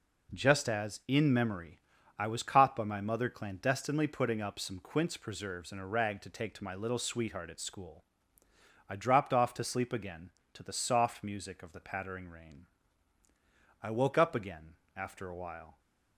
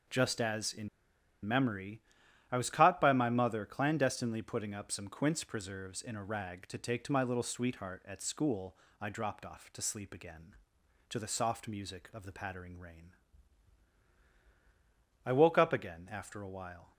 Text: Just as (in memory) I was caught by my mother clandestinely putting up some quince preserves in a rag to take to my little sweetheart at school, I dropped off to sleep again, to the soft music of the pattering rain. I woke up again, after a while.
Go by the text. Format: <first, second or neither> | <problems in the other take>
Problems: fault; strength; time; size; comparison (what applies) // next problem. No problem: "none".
first | pauses between "in" and "memory"; noticeable; at 0.8 s; 0.56 s long